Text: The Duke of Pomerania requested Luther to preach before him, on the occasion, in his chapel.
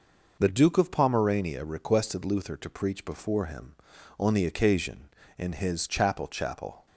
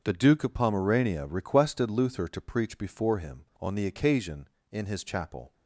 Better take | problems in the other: second | says "chapel" twice; at 6.2 s

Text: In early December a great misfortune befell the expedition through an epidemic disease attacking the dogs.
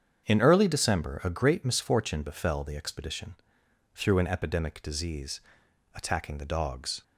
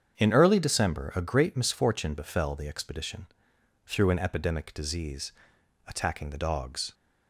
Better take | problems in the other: neither | starts louder than the rest; strong; the same in both // pauses between "expedition" and "through"; noticeable; the same in both // pauses between "disease" and "attacking"; noticeable; the same in both

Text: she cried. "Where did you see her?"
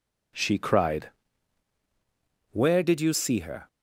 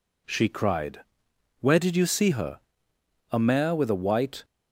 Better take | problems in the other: first | goes on to say "A mare with a white"; noticeable; from 3.3 s on; 1.1 s long

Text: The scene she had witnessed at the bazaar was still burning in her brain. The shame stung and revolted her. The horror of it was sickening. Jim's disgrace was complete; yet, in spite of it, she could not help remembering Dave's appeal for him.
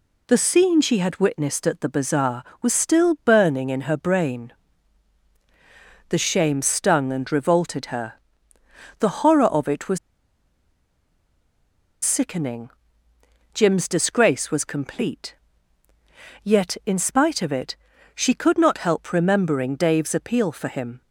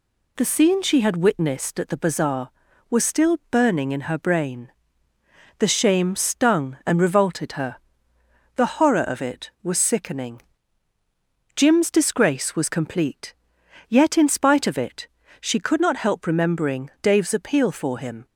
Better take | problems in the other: second | pauses between "was" and "sickening"; strong; at 9.9 s; 2.0 s long

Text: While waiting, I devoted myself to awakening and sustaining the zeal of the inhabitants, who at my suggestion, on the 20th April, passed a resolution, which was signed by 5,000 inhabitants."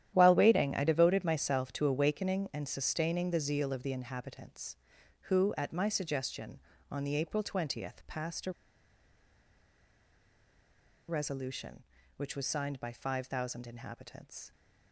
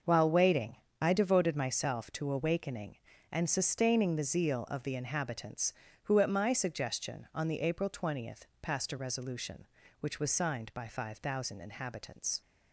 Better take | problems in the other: second | starts louder than the rest; strong; until 1.1 s; 11 dB; also in the second // pauses between "a" and "resolution"; strong; at 8.5 s; 2.5 s long

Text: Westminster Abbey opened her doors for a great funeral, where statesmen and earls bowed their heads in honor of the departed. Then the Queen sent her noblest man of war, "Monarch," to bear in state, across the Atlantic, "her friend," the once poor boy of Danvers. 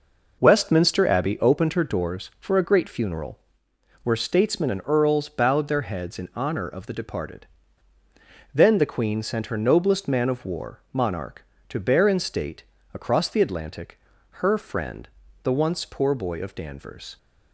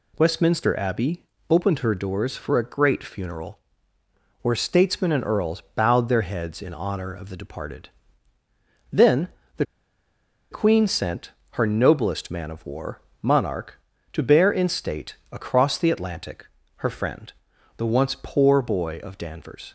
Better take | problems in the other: first | pauses between "Abbey" and "opened"; slight; at 1.2 s; 0.26 s long // pauses between "Then" and "the"; slight; at 9.2 s; 0.30 s long // pauses between "the" and "Queen"; noticeable; at 9.6 s; 0.86 s long // pauses between "sent" and "her"; slight; at 11.3 s; 0.20 s long

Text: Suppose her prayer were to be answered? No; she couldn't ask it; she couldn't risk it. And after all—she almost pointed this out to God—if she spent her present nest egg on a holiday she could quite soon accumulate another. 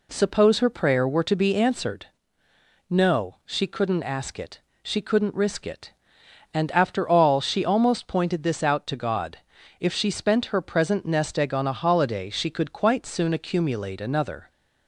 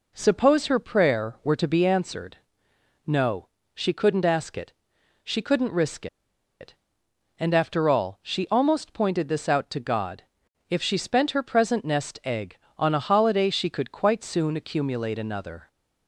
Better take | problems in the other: first | pauses between "risk" and "it"; noticeable; at 6.0 s; 0.54 s long

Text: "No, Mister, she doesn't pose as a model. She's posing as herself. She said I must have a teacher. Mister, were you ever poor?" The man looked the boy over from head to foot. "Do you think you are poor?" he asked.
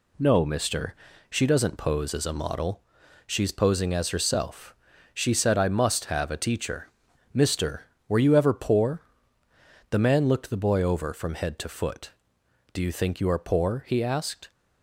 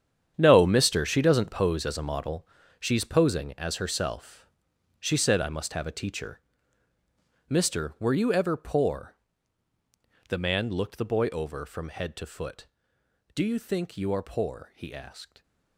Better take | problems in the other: first | gets quieter; strong; throughout; 13 dB

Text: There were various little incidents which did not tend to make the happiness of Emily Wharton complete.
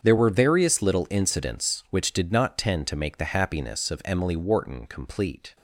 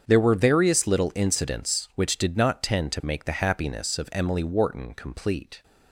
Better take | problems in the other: neither | starts louder than the rest; strong; the same in both

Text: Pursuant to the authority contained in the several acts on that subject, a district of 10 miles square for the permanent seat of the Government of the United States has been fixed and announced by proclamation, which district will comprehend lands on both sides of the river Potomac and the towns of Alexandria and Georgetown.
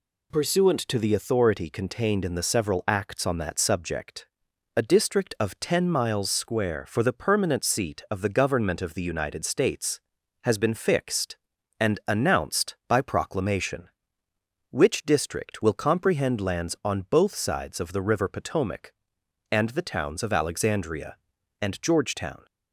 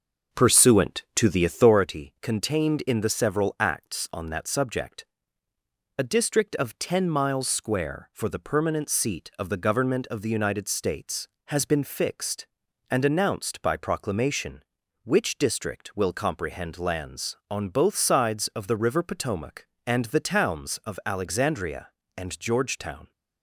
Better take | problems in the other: first | starts louder than the rest; until 1.8 s; 6 dB

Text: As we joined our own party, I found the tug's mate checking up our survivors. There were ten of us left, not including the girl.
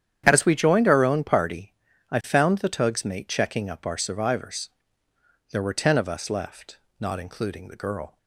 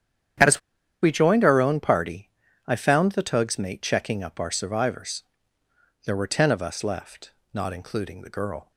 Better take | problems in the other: first | starts louder than the rest; strong; until 1.8 s; 9.5 dB; strong in the first // pauses between "As" and "we"; at 0.6 s; 0.42 s long

